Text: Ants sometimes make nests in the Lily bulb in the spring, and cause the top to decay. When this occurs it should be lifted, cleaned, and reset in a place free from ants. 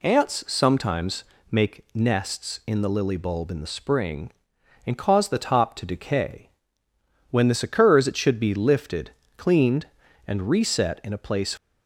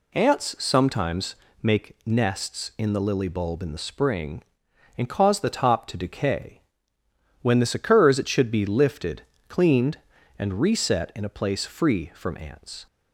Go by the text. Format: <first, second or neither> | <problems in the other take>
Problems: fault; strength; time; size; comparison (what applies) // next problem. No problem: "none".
second | pauses between "sometimes" and "make"; slight; at 1.2 s; 0.28 s long; slight in the second // stops before "free from ants"; at 11.5 s